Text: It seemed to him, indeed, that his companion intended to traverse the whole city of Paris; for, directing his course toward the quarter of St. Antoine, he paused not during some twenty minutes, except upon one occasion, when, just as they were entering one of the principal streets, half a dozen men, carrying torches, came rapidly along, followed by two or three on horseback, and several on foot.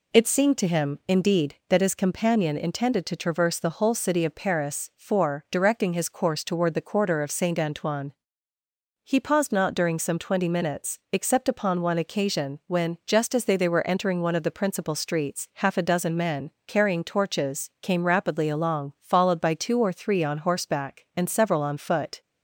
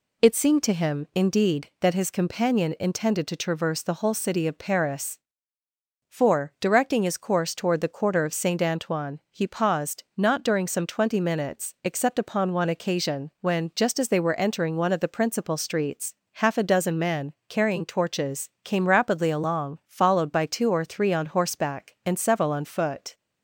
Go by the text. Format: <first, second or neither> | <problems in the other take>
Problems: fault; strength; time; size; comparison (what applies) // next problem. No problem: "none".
second | says "they" twice; at 13.5 s